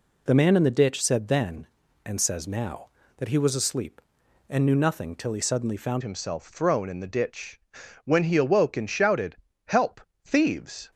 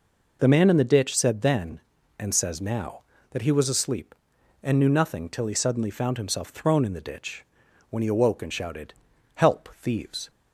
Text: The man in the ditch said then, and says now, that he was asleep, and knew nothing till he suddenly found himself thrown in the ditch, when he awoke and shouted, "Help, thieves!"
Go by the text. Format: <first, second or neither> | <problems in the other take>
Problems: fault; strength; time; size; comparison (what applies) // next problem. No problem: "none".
second | changes voice at "himself"; from 6.0 s on; 4.9 s long